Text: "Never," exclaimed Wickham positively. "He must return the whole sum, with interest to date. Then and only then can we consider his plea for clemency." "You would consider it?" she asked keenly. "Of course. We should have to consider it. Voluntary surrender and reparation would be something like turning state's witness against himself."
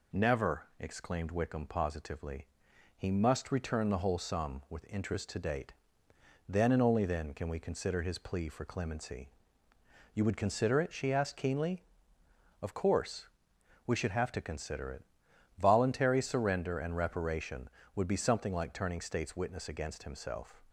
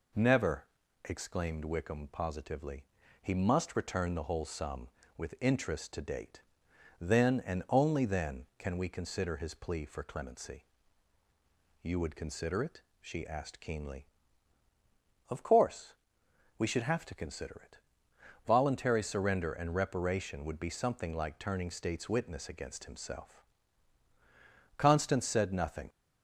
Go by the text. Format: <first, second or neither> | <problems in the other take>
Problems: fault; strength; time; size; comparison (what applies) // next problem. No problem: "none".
first | goes on to say "Constance said nothing"; noticeable; from 24.7 s on; 1.1 s long